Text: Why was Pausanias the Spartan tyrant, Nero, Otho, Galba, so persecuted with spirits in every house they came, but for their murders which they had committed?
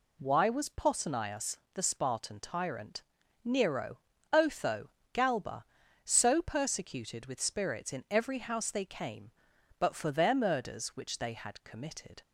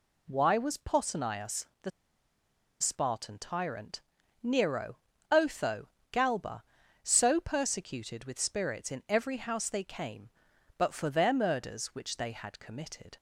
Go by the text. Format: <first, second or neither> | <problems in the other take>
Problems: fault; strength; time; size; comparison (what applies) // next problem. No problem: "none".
first | pauses between "Pausanias" and "the"; slight; at 1.6 s; 0.16 s long; slight in the first // pauses between "the" and "Spartan"; noticeable; at 1.9 s; 0.90 s long